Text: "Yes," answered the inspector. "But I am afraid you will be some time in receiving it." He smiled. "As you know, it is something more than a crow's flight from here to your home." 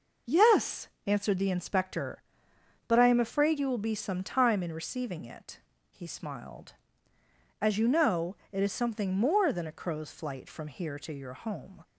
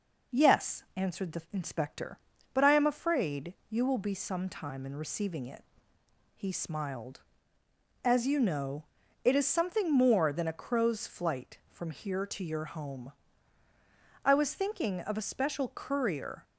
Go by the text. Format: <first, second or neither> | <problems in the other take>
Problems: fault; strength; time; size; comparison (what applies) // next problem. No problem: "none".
first | pauses between "afraid" and "you"; slight; at 3.5 s; 0.16 s long // goes on to say "I was thinking of a special courier"; strong; from 14.2 s on; 2.2 s long